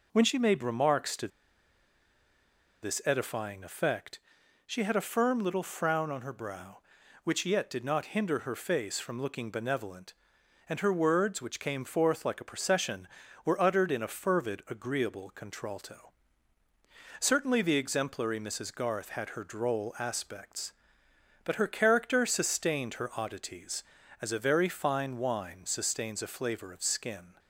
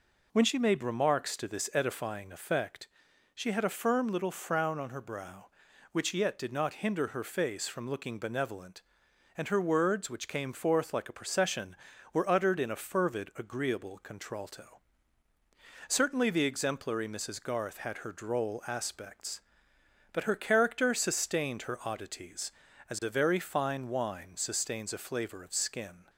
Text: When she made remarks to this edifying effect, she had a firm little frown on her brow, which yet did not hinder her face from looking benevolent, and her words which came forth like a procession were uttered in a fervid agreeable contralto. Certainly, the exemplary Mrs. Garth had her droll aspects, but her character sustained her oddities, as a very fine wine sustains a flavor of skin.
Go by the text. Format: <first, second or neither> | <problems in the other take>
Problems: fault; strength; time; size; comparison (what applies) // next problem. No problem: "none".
second | pauses between "to" and "this"; strong; at 1.2 s; 1.5 s long